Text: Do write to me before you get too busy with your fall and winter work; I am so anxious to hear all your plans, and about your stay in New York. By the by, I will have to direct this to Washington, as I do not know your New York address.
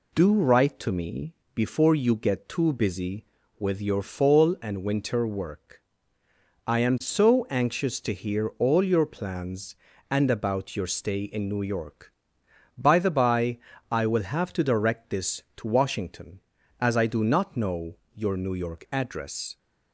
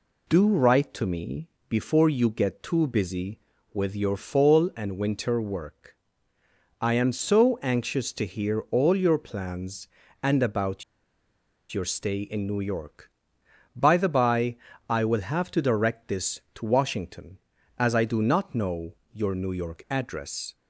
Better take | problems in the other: first | pauses between "me" and "before"; slight; at 1.4 s; 0.22 s long; slight in the first // pauses between "about" and "your"; noticeable; at 10.8 s; 0.88 s long // pauses between "know" and "your"; slight; at 18.9 s; 0.16 s long; slight in the first

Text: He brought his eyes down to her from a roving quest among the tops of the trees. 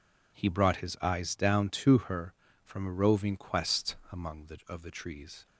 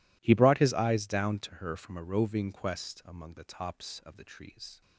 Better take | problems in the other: second | pauses between "quest" and "among"; slight; at 3.9 s; 0.16 s long // skips "tops"; at 4.6 s

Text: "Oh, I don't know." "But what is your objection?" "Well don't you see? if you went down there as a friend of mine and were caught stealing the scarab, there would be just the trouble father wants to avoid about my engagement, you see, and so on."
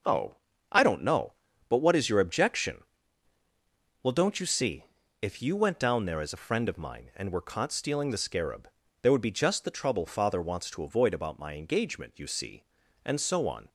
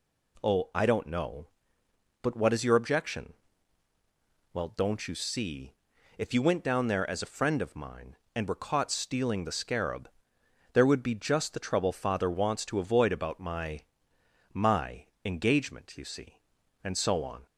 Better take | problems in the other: first | says "my" twice; at 14.5 s

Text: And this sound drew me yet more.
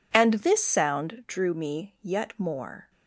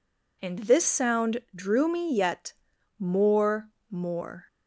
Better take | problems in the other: first | pauses between "yet" and "more"; noticeable; at 2.5 s; 0.46 s long // says "more" twice; at 3.8 s

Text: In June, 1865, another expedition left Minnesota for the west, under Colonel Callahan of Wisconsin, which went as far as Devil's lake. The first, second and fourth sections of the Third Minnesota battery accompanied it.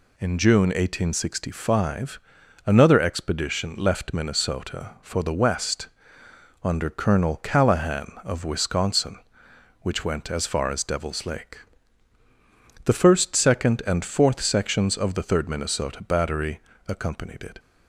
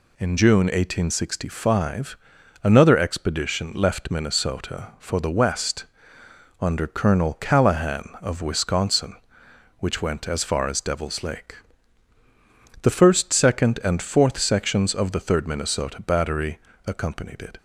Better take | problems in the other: neither | pauses between "battery" and "accompanied"; slight; the same in both

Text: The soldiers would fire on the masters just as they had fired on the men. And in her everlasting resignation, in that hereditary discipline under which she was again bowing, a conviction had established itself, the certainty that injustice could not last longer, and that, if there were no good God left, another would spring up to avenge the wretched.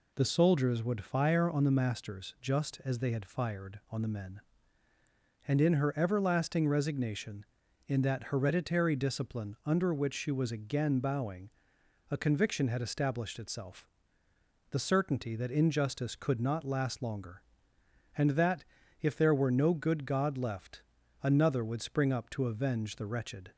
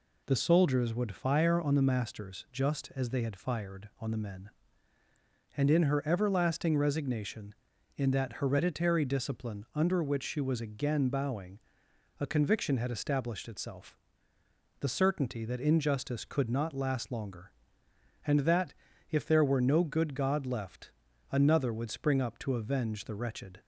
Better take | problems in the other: neither | none

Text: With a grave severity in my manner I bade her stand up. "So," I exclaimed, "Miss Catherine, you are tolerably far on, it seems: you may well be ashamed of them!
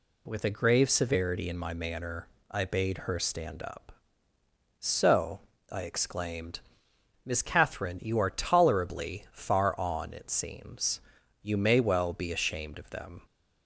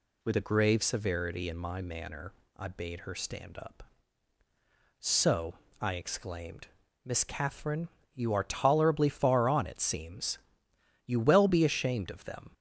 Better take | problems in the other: first | pauses between "manner" and "I"; slight; at 2.3 s; 0.26 s long; slight in the first // skips "may"; at 11.1 s

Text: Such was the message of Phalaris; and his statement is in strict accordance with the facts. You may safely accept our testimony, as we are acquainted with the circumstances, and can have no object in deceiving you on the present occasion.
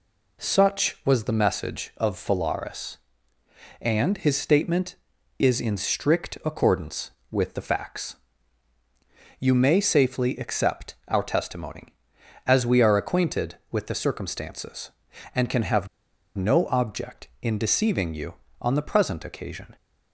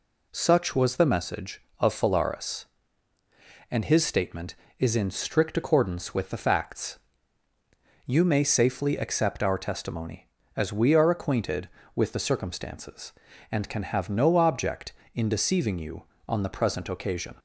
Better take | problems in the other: second | pauses between "have" and "no"; noticeable; at 15.8 s; 0.49 s long

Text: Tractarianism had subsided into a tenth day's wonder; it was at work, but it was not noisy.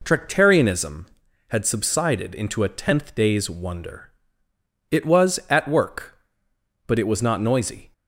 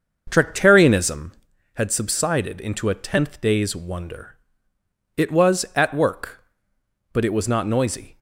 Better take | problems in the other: first | starts louder than the rest; until 1.5 s; 6.5 dB

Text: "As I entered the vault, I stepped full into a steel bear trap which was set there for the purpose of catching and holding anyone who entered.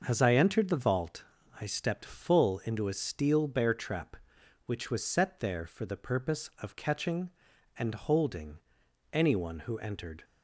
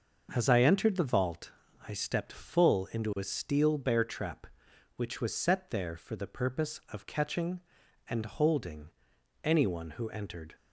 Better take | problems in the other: neither | starts louder than the rest; the same in both // pauses between "holding" and "anyone"; noticeable; the same in both

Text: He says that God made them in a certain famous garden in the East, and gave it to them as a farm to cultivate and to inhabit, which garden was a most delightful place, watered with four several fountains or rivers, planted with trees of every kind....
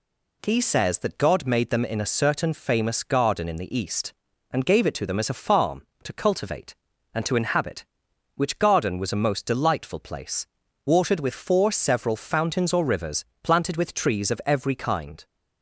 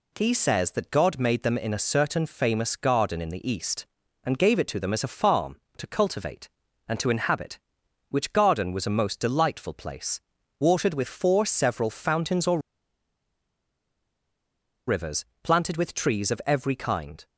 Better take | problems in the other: first | pauses between "or" and "rivers"; strong; at 12.5 s; 2.2 s long

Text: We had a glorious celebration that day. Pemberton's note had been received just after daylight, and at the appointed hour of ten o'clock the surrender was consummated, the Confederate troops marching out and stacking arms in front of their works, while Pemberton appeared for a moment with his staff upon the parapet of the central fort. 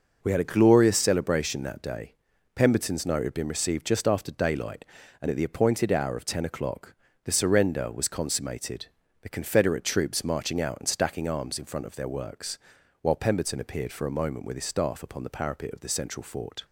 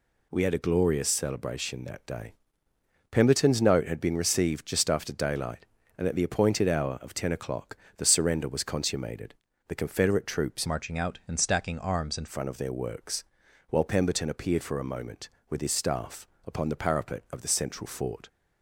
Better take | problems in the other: first | pauses between "o'clock" and "the"; slight; at 7.7 s; 0.20 s long; slight in the first // changes voice from "marching" to "in"; from 10.6 to 12.2 s; 1.6 s long // pauses between "staff" and "upon"; slight; at 16.2 s; 0.20 s long

